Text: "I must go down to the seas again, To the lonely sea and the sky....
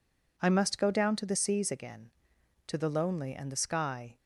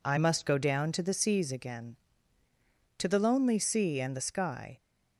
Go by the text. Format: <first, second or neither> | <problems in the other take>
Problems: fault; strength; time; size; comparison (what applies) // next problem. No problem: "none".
second | skips "sea"; at 3.3 s